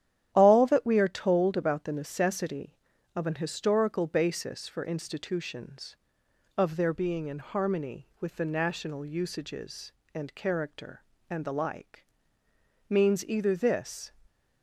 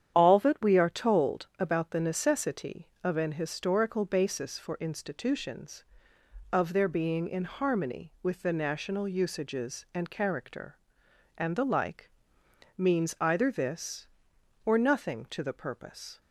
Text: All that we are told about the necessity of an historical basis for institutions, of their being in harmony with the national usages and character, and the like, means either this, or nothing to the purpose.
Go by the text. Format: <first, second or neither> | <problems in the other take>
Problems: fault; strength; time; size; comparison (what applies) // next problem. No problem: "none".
second | starts louder than the rest; strong; until 1.3 s; 10.5 dB; strong in the second // stops before "or nothing to the purpose"; at 14.2 s